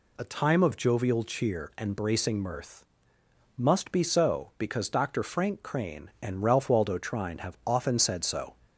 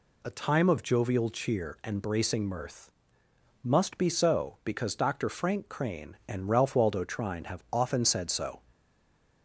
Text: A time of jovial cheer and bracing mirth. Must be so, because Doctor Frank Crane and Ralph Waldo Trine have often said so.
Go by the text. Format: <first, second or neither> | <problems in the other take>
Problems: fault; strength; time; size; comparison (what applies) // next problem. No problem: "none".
first | stays silent after the last word; slight; from 8.7 s on; 0.7 s long